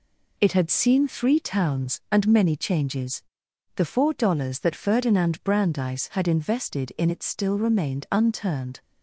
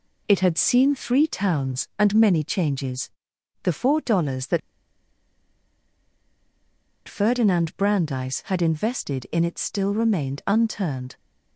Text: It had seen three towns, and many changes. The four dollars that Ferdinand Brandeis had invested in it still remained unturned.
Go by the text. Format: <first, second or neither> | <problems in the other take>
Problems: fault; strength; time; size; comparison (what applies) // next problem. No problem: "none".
first | pauses between "that" and "Ferdinand"; strong; at 4.5 s; 2.4 s long